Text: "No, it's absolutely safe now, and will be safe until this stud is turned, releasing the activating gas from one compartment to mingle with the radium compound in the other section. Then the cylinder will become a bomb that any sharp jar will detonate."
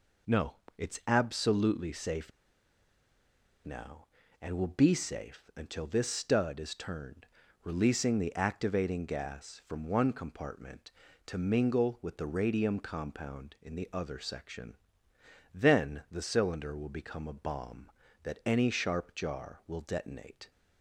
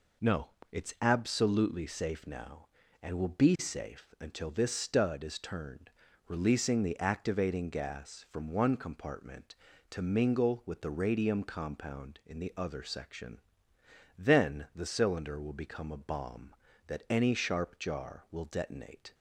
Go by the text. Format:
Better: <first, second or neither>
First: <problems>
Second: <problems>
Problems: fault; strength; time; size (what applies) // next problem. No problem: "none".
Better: second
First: pauses between "safe" and "now"; strong; at 2.3 s; 1.3 s long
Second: none